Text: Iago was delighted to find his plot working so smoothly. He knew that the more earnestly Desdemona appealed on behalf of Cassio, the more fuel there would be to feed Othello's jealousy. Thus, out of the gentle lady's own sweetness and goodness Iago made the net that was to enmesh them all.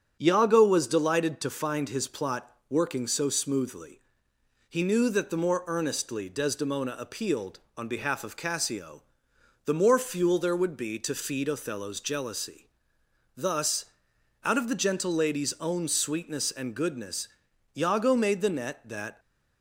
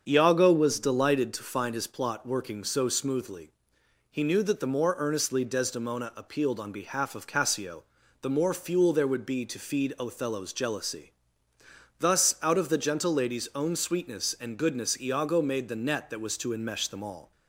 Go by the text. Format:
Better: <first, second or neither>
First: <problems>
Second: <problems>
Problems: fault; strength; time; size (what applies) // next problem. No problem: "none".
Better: second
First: starts louder than the rest; strong; until 1.2 s; 7 dB // pauses between "plot" and "working"; slight; at 2.5 s; 0.18 s long // pauses between "goodness" and "Iago"; noticeable; at 17.2 s; 0.48 s long // stops before "was to enmesh them all"; at 19.1 s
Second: starts louder than the rest; until 1.0 s; 7 dB